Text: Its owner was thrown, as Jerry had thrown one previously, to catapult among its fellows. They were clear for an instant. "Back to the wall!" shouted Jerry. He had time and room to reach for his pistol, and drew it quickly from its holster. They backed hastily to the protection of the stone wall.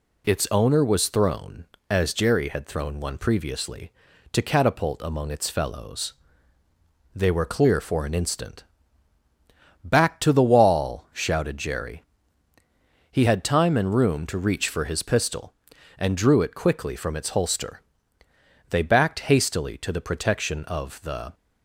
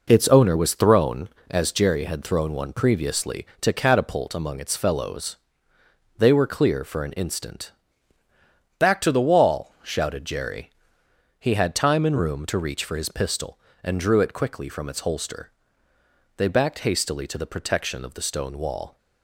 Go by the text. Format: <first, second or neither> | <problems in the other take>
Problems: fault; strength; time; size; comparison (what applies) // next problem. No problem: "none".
second | stops before "stone wall"; at 21.3 s